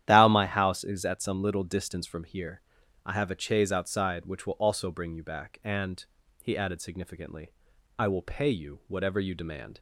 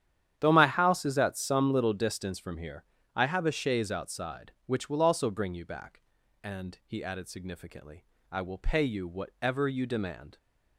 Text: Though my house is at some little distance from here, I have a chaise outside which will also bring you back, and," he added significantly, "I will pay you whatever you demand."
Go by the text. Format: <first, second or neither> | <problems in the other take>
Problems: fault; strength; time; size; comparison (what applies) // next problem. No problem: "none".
second | starts louder than the rest; strong; until 1.0 s; 11 dB; strong in the second // says "Thou" for "Though"; at 0.0 s